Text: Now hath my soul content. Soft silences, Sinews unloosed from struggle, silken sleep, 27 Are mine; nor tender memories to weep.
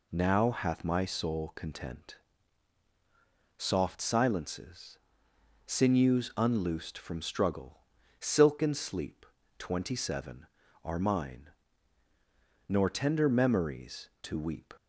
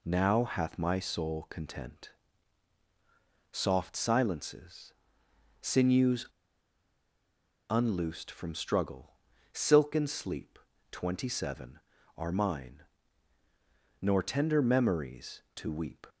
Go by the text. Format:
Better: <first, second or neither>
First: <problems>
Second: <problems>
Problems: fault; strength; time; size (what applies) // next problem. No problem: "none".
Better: first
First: none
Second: pauses between "Sinews" and "unloosed"; strong; at 6.2 s; 1.4 s long